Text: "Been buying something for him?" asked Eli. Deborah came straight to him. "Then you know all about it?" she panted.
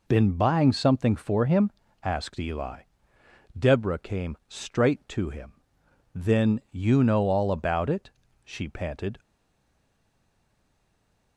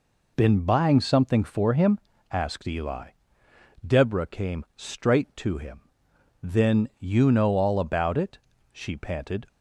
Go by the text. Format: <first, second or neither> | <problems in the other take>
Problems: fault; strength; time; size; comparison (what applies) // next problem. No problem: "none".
second | stays silent after the last word; from 9.1 s on; 2.2 s long